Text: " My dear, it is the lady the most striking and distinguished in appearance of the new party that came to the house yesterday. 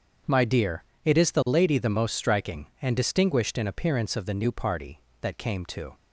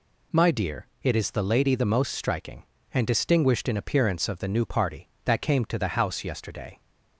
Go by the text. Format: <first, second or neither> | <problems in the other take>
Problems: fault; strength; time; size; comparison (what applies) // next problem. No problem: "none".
second | stops before "the house yesterday"; at 5.9 s